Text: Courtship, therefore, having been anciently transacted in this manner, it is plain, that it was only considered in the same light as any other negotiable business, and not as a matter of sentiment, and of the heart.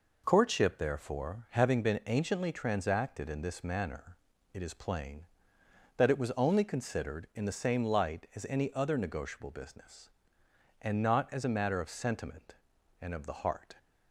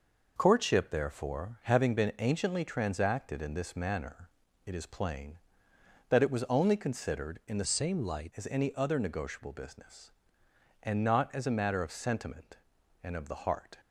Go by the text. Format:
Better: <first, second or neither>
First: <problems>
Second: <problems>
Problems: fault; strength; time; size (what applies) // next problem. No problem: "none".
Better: first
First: none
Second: changes voice from "same" to "light"; from 7.6 to 8.3 s; 0.7 s long